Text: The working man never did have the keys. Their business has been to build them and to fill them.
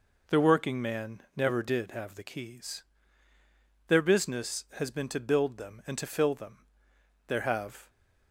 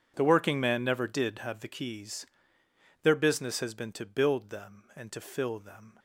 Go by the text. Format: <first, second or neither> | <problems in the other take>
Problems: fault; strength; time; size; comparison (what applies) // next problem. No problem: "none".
second | goes on to say "There have"; noticeable; from 7.2 s on; 0.62 s long